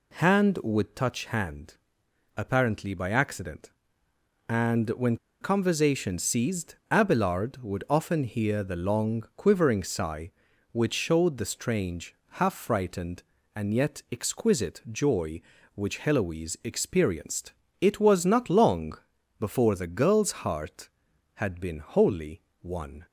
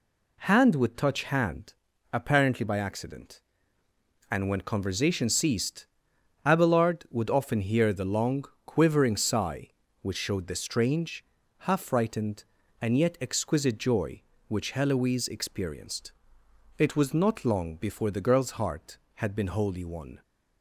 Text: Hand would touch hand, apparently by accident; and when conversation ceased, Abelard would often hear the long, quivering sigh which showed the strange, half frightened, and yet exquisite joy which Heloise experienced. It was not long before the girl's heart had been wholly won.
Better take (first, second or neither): second